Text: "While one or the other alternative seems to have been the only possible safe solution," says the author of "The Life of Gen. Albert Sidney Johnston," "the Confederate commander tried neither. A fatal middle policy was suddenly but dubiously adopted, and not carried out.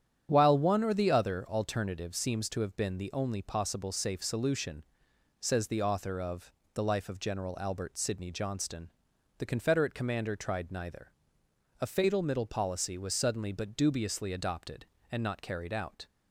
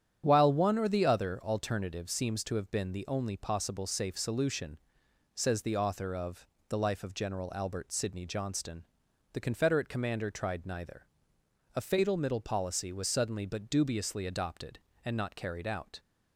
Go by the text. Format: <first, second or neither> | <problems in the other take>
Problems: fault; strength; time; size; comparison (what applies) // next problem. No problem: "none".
neither | starts louder than the rest; strong; the same in both // pauses between "of" and "The"; slight; the same in both